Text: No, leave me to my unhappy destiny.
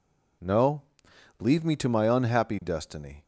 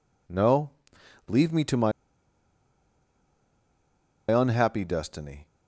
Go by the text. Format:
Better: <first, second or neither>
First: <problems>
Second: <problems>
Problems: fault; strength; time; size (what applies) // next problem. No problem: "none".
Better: first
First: none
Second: pauses between "my" and "unhappy"; strong; at 1.9 s; 2.4 s long